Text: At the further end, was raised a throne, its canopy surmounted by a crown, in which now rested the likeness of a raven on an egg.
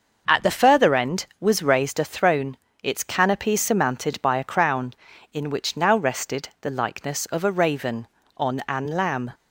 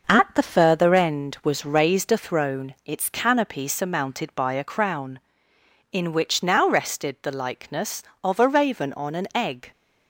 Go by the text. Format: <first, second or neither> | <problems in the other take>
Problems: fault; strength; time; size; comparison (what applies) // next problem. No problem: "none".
second | starts louder than the rest; noticeable; until 1.4 s; 6 dB // says "lamb" for "egg"; at 8.8 s